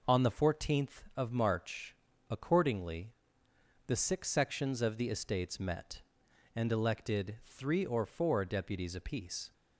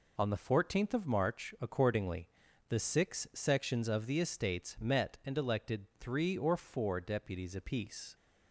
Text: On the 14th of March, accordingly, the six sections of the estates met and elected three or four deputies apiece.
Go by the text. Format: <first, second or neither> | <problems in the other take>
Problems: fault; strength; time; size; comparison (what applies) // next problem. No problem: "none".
neither | none